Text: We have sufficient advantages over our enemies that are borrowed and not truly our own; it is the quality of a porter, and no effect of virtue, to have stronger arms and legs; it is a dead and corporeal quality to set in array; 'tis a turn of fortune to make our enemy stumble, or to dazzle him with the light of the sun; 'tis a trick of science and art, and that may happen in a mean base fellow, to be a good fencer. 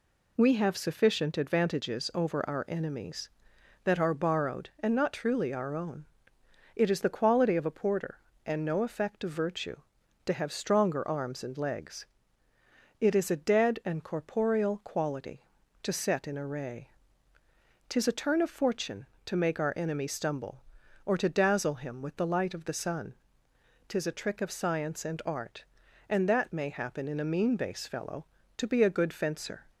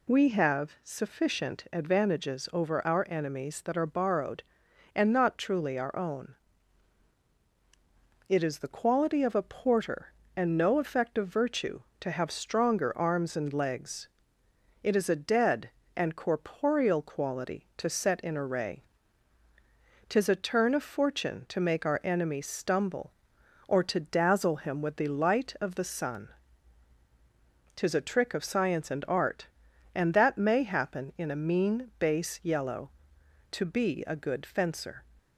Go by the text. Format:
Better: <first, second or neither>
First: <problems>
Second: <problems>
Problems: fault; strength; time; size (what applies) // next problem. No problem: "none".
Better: first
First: none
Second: says "yellow" for "fellow"; at 32.4 s